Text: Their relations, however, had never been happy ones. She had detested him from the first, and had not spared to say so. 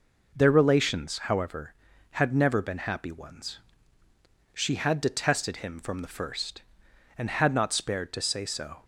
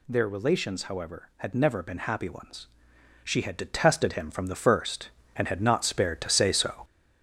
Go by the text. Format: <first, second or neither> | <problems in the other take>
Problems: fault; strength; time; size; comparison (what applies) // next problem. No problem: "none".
first | gets louder; noticeable; throughout; 6 dB